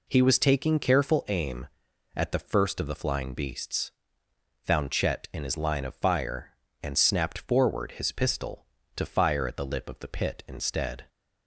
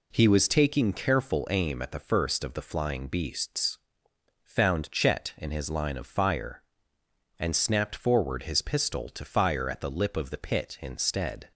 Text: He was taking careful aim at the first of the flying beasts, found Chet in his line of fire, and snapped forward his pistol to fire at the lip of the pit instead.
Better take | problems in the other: neither | none

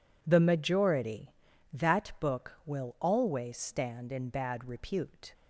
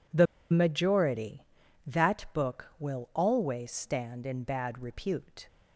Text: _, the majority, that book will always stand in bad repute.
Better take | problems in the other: first | pauses between "the" and "majority"; slight; at 0.2 s; 0.25 s long

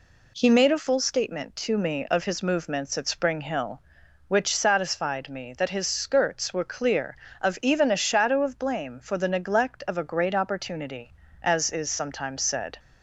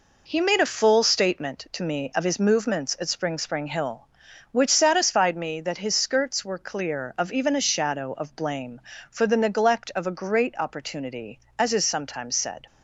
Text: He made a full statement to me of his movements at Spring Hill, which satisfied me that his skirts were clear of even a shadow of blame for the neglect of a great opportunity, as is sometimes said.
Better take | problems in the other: first | says "Spring" twice; at 3.3 s

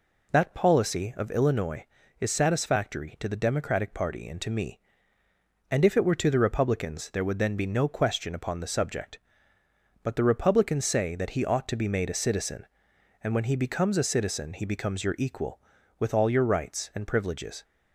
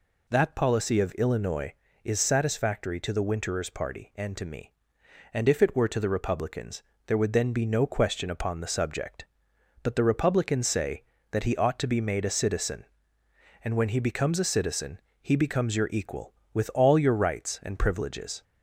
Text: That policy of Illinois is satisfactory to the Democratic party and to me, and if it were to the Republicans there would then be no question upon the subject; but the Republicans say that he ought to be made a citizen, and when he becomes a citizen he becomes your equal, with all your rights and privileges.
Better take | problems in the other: first | says "Winterers" for "Democratic"; at 3.2 s // pauses between "Republicans" and "there"; slight; at 6.8 s; 0.24 s long // pauses between "citizen" and "he"; slight; at 14.9 s; 0.22 s long

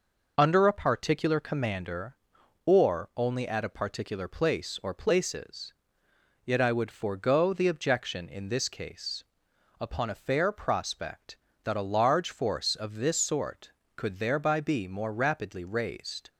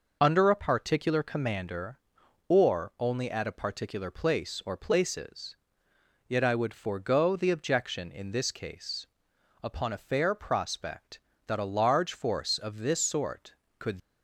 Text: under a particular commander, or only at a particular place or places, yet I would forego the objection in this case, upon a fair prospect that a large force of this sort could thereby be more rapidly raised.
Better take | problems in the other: first | stops before "thereby be more rapidly raised"; at 14.0 s

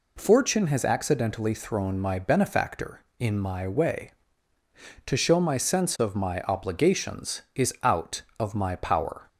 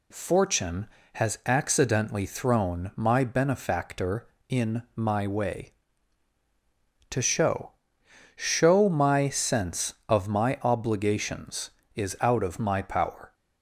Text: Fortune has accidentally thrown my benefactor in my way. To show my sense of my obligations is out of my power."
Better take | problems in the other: first | says "show" twice; at 8.3 s

